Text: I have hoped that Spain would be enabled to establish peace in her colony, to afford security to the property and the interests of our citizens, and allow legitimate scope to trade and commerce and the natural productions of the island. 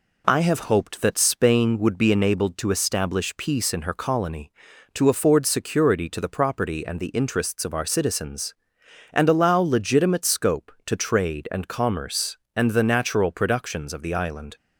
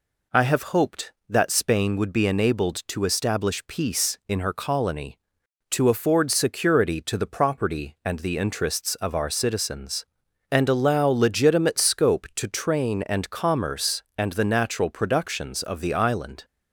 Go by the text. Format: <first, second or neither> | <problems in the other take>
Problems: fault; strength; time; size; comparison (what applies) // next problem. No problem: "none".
first | says "train" for "trade"; at 12.4 s